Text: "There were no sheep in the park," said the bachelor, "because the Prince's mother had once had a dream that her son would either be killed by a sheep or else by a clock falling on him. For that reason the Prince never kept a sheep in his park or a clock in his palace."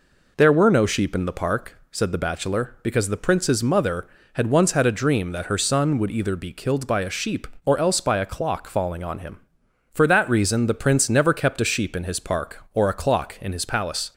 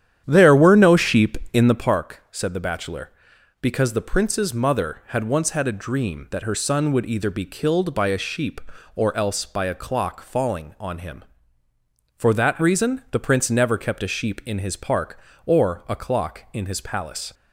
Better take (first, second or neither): first